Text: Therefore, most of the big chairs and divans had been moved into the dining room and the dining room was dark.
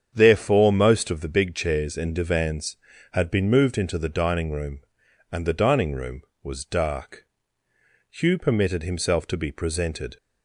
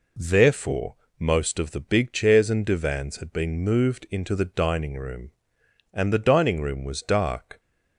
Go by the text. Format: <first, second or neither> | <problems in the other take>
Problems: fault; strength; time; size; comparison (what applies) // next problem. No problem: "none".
second | starts louder than the rest; strong; until 1.1 s; 7.5 dB // goes on to say "Hugh permitted himself to be presented"; strong; from 8.1 s on; 2.0 s long